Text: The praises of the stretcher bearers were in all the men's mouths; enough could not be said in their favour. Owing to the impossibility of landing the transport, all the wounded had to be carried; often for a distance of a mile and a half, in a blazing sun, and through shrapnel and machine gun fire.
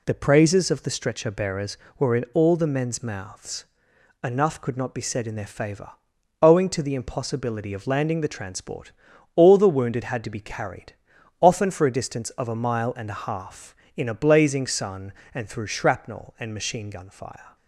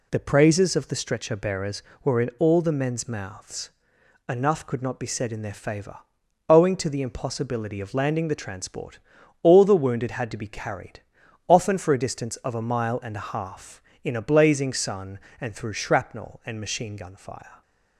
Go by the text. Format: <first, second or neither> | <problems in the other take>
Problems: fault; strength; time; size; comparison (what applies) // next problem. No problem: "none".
neither | none